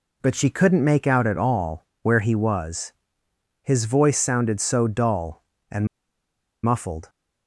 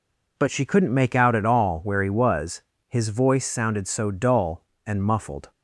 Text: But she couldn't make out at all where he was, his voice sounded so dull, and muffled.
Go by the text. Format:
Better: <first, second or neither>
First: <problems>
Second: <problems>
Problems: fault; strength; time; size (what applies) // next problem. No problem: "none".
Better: second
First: pauses between "all" and "where"; slight; at 1.8 s; 0.18 s long // pauses between "and" and "muffled"; noticeable; at 5.8 s; 0.76 s long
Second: none